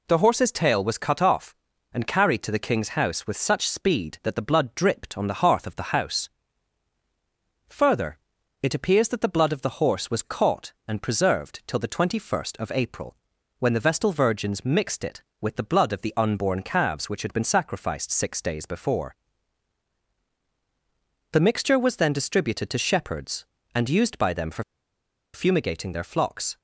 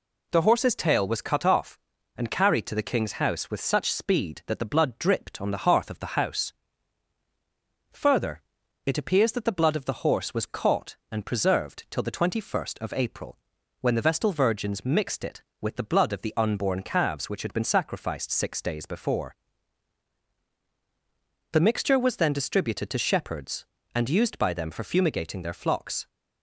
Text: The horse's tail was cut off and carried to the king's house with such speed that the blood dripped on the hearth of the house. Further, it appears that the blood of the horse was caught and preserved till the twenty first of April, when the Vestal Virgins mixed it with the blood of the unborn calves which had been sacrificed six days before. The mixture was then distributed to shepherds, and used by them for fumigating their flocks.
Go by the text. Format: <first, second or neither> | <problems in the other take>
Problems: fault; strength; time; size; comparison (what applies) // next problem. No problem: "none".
second | pauses between "for" and "fumigating"; noticeable; at 24.6 s; 0.70 s long